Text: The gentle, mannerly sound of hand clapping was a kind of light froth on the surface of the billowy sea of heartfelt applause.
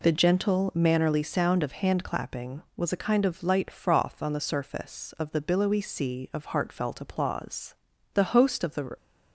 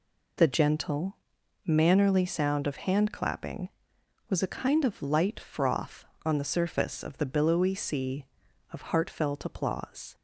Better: second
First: goes on to say "The host of the"; noticeable; from 8.1 s on; 0.82 s long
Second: none

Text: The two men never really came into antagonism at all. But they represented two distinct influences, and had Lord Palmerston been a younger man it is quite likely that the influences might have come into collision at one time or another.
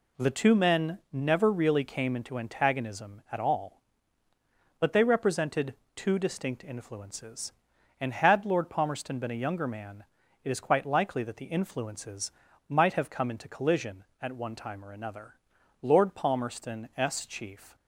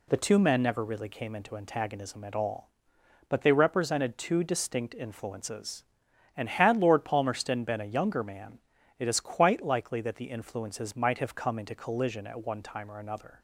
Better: second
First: pauses between "represented" and "two"; slight; at 5.7 s; 0.22 s long // pauses between "man" and "it"; at 10.0 s; 0.40 s long // pauses between "influences" and "might"; at 12.3 s; 0.38 s long // goes on to say "Lord Palmerston s chief"; strong; from 15.8 s on; 1.9 s long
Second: pauses between "man" and "it"; at 8.5 s; 0.38 s long

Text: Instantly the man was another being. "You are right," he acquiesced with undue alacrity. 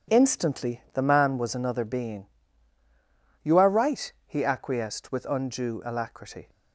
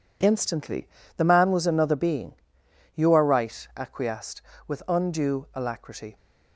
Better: first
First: none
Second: pauses between "Instantly" and "the"; slight; at 0.8 s; 0.28 s long // skips "he"; at 3.7 s

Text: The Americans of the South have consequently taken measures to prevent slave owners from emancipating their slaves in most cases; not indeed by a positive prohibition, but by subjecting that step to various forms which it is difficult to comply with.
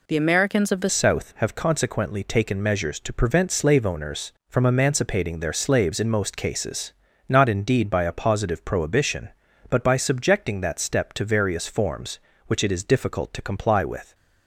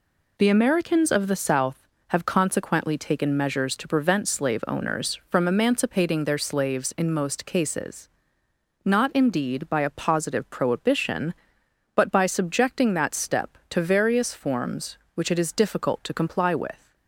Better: second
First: changes voice at "South"; from 0.8 s on; 13.3 s long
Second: none

